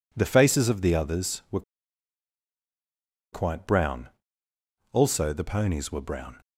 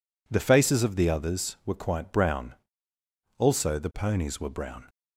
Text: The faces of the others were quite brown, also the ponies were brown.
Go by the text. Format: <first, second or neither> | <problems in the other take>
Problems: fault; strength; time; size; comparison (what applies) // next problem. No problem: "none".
second | pauses between "were" and "quite"; strong; at 1.6 s; 1.7 s long